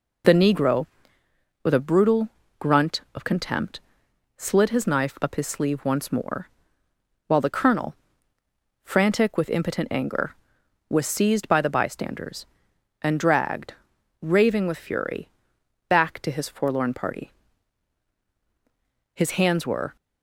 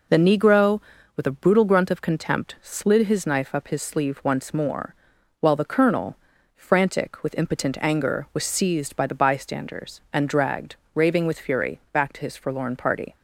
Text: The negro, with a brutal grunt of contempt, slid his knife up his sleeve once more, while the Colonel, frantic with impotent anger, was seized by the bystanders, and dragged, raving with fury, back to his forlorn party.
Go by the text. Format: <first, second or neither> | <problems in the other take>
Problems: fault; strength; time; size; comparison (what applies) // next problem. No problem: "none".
second | pauses between "brutal" and "grunt"; slight; at 2.2 s; 0.28 s long // goes on to say "His hands were"; noticeable; from 19.1 s on; 0.82 s long